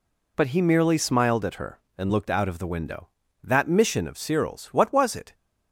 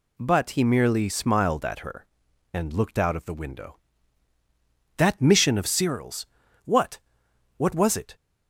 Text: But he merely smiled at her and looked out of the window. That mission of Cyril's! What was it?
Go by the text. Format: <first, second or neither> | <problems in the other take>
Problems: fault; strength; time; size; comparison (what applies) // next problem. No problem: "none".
first | says "What" twice; at 7.5 s